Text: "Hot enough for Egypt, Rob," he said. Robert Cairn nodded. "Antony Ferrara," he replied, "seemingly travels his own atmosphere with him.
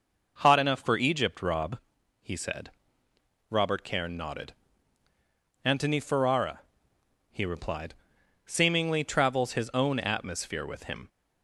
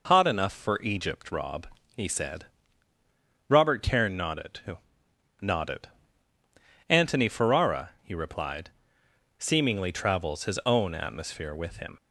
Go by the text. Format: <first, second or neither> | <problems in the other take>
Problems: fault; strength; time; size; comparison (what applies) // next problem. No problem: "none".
first | says "nodded" twice; at 5.4 s